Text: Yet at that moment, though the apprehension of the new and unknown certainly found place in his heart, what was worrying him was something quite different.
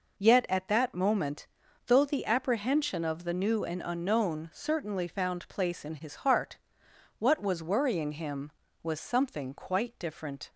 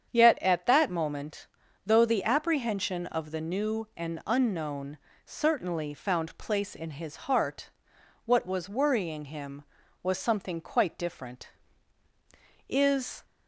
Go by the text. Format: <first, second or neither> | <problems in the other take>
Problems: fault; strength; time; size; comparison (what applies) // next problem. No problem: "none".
first | starts louder than the rest; strong; until 1.1 s; 8 dB // pauses between "unknown" and "certainly"; slight; at 4.9 s; 0.28 s long // goes on to say "Is"; from 12.6 s on; 0.56 s long